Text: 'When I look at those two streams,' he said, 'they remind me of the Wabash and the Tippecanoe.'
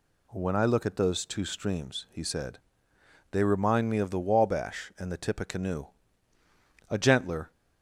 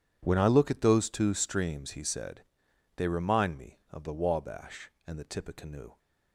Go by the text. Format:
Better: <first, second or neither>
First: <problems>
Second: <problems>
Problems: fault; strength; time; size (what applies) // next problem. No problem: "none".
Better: second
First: goes on to say "A gentler"; noticeable; from 6.8 s on; 0.62 s long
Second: none